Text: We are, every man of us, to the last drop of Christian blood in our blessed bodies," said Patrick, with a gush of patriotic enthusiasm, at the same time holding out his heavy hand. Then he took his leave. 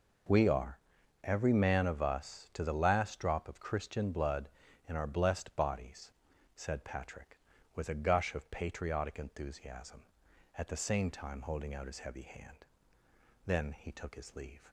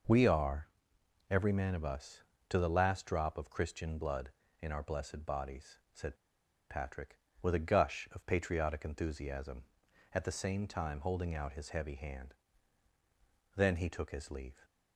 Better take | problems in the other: first | pauses between "said" and "Patrick"; noticeable; at 6.1 s; 0.54 s long

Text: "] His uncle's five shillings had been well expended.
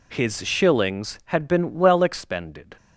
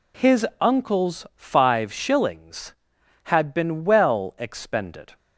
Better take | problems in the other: second | skips "uncle's five"; at 0.4 s

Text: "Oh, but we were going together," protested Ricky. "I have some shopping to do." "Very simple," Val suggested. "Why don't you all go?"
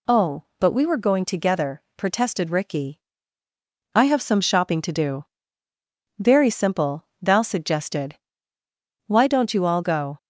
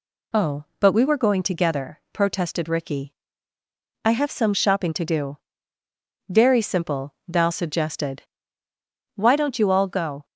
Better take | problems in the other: neither | none

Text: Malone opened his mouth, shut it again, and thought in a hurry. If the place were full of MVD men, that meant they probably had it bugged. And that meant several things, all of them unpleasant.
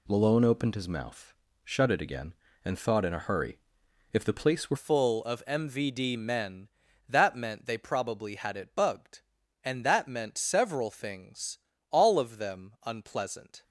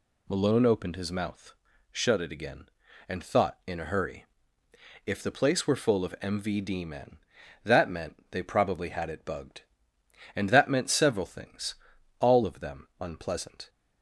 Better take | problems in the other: second | changes voice at "full"; from 4.7 s on; 8.9 s long

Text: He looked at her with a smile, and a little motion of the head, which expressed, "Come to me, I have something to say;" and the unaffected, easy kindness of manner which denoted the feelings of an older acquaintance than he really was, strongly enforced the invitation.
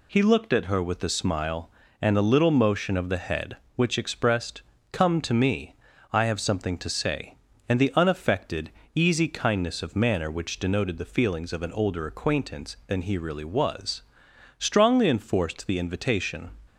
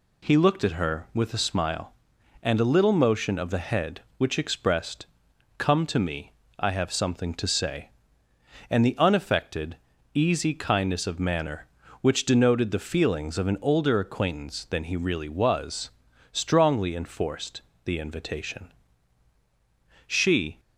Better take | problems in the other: first | pauses between "enforced" and "the"; slight; at 17.5 s; 0.24 s long // goes on to say "She"; from 20.0 s on; 0.52 s long

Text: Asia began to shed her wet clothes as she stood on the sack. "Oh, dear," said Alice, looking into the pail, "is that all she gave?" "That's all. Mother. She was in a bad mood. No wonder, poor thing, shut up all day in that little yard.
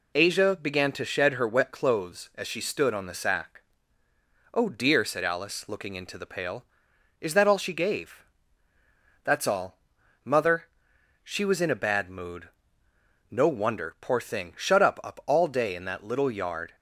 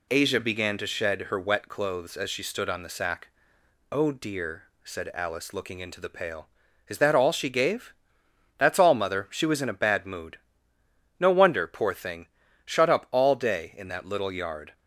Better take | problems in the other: second | says "up" twice; at 15.0 s

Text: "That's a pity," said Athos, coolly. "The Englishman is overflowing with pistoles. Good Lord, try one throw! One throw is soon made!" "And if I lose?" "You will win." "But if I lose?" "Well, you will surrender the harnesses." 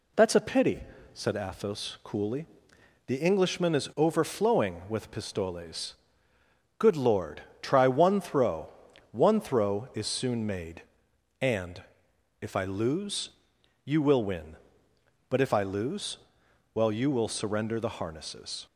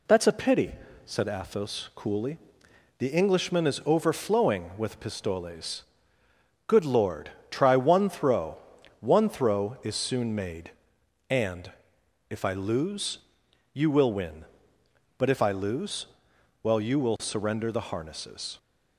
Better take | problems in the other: neither | pauses between "And" and "if"; noticeable; the same in both

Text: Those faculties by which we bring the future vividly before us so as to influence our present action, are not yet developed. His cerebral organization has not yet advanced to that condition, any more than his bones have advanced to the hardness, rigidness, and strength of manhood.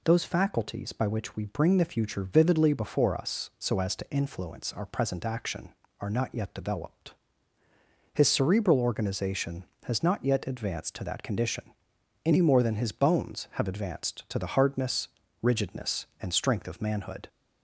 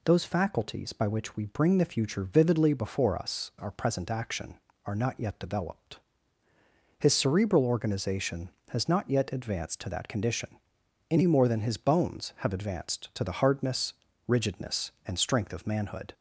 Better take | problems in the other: first | skips "so as to influence"; at 3.5 s

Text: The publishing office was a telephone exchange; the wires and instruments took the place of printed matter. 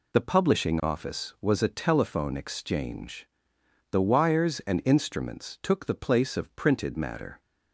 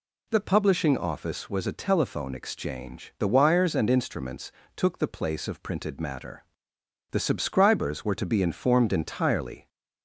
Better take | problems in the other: first | pauses between "instruments" and "took"; slight; at 4.5 s; 0.24 s long // goes on to say "The subscribers were to be informed entirely"; strong; from 7.1 s on; 2.5 s long

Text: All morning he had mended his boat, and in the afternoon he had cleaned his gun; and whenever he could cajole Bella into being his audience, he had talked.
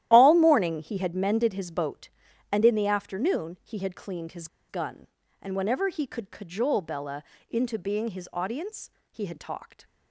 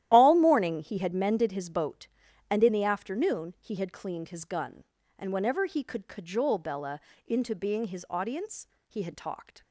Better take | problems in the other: second | starts louder than the rest; strong; until 1.1 s; 12.5 dB; strong in the second // pauses between "his" and "gun"; slight; at 4.4 s; 0.23 s long // pauses between "Bella" and "into"; slight; at 7.2 s; 0.28 s long; slight in the second

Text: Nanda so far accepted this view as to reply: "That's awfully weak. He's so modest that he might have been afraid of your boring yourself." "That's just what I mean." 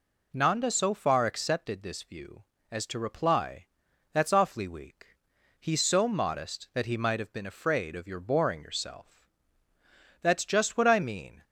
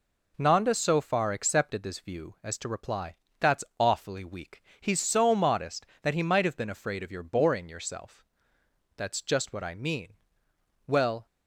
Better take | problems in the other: first | pauses between "That's" and "awfully"; slight; at 3.6 s; 0.16 s long // goes on to say "Well"; slight; from 10.8 s on; 0.38 s long

